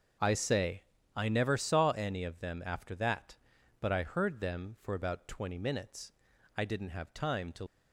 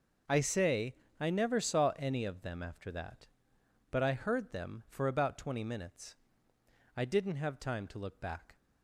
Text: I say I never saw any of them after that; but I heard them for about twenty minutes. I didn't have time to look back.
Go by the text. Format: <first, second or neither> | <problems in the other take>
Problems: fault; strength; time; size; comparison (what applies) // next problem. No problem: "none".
second | starts louder than the rest; until 1.5 s; 6.5 dB // pauses between "say" and "I"; slight; at 0.8 s; 0.32 s long; slight in the second // stops before "look back"; at 7.6 s